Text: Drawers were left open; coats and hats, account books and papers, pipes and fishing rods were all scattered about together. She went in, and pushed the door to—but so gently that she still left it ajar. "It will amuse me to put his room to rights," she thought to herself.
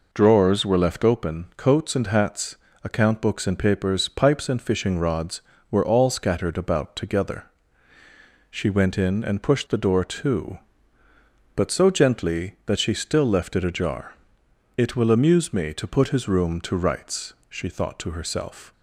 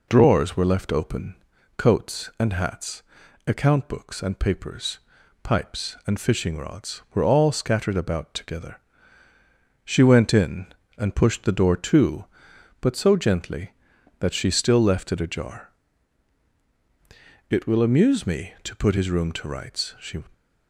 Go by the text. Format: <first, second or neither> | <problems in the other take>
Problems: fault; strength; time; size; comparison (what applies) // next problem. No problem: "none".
first | stops before "thought to herself"; at 20.3 s